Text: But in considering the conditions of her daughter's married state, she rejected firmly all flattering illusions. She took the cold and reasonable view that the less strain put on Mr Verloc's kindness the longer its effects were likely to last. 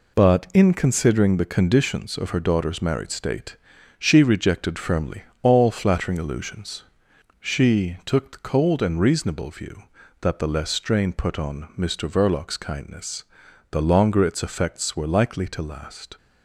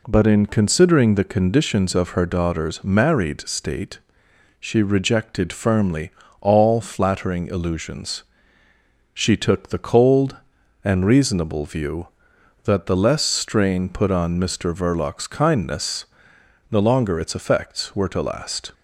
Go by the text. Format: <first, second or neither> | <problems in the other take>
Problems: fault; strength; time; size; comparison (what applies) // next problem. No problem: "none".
first | pauses between "firmly" and "all"; slight; at 6.1 s; 0.30 s long; slight in the first // pauses between "kindness" and "the"; noticeable; at 16.0 s; 0.64 s long; noticeable in the first // skips "likely"; at 18.0 s